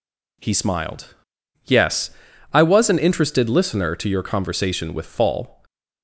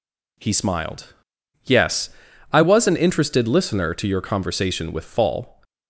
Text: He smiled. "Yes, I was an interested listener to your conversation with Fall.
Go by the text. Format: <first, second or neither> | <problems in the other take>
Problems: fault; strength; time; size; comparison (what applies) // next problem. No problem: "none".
neither | none